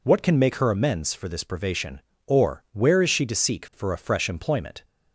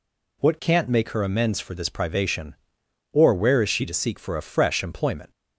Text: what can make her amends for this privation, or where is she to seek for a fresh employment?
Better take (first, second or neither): first